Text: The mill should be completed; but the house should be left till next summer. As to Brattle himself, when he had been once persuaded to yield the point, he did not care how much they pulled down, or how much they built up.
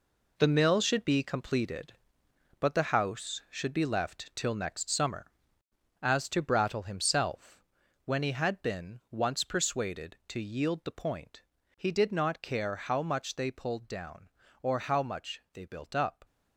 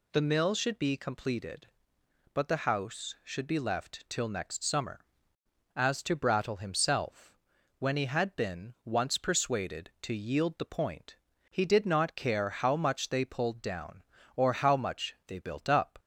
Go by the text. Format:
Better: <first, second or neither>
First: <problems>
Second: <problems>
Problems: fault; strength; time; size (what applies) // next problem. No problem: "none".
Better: second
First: gets quieter; strong; throughout; 9 dB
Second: none